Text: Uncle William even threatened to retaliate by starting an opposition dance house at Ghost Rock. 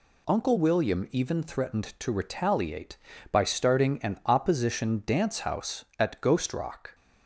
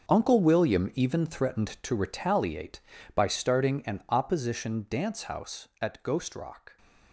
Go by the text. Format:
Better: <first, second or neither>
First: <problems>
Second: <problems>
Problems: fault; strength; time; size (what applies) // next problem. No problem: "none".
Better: first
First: none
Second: gets quieter; strong; throughout; 13 dB